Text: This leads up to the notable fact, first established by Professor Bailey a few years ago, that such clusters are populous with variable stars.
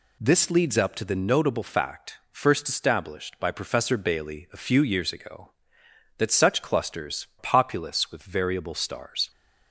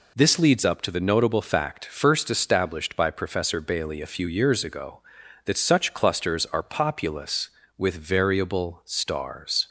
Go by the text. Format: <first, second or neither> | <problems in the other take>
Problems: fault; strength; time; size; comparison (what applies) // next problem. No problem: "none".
second | skips "are"; at 7.3 s